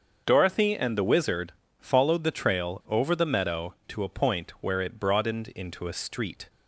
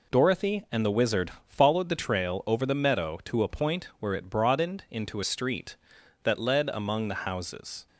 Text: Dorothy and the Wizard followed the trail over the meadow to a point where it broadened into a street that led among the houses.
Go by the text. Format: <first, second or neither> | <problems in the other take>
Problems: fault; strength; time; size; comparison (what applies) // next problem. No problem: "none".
second | starts louder than the rest; until 1.2 s; 6.5 dB // pauses between "Wizard" and "followed"; slight; at 1.5 s; 0.28 s long // stops before "that led among the houses"; at 6.4 s